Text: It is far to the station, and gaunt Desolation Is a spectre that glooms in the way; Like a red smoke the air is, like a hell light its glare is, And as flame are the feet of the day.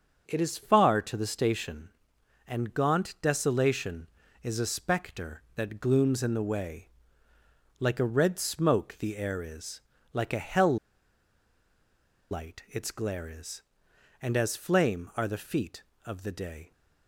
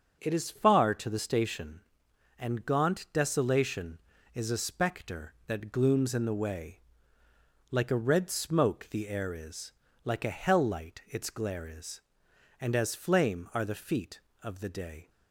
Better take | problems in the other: second | starts louder than the rest; until 1.2 s; 6.5 dB; also in the second // pauses between "hell" and "light"; strong; at 10.7 s; 1.5 s long

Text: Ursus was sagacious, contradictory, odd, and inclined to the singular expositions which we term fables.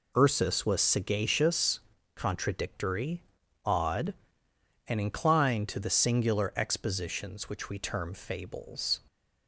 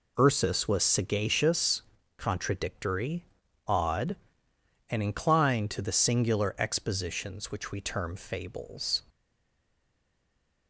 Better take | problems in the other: first | stays silent after the last word; noticeable; from 9.0 s on; 1.6 s long

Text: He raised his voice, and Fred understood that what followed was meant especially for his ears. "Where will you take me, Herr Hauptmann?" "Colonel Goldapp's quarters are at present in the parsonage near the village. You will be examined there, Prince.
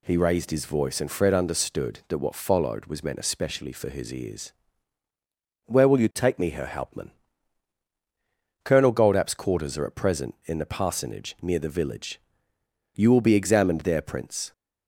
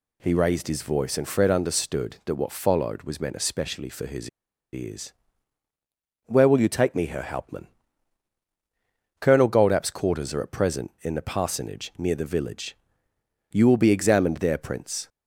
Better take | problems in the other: first | pauses between "his" and "ears"; at 4.2 s; 0.43 s long

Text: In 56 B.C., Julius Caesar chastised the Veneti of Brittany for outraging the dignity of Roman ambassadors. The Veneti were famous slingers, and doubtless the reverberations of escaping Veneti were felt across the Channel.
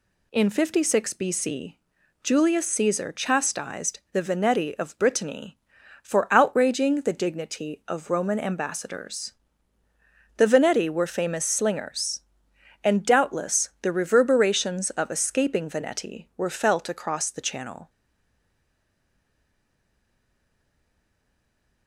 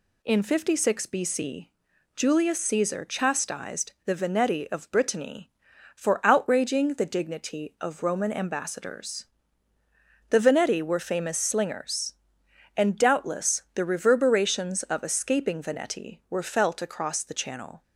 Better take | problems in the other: second | stays silent after the last word; strong; from 17.8 s on; 4.0 s long

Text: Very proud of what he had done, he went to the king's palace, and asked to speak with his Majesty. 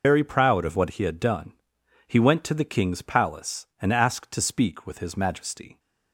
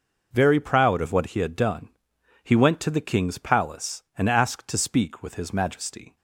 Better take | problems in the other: second | loses the start of "Very"; at 0.0 s; 95 ms

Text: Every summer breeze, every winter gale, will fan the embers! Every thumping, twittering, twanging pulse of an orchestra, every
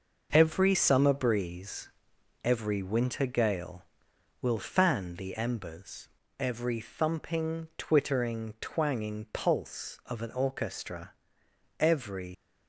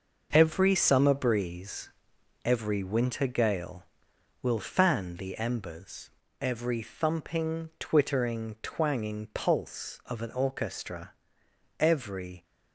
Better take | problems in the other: second | leaves "every" unfinished; at 12.3 s; 85 ms

